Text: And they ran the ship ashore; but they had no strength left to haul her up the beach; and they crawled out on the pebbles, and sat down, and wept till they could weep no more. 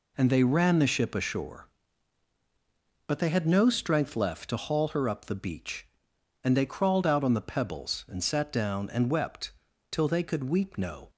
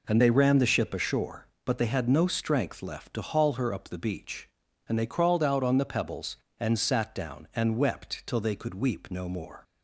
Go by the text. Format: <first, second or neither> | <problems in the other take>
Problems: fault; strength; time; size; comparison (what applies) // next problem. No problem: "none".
second | pauses between "wept" and "till"; at 9.5 s; 0.40 s long // stops before "more"; at 11.0 s